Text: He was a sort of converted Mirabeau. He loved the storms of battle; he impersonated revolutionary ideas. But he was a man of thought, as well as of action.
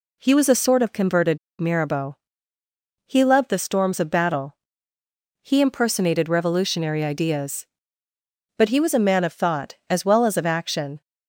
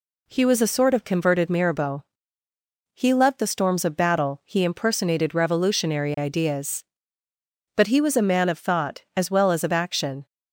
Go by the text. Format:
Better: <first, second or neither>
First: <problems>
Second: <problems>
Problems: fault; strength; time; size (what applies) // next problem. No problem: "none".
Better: second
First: pauses between "converted" and "Mirabeau"; slight; at 1.3 s; 0.20 s long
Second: none